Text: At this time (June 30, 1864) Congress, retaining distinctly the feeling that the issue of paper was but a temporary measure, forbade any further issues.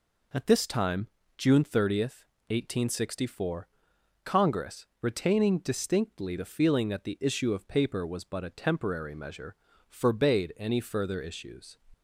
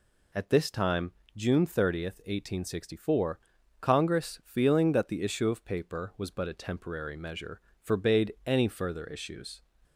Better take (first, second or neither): first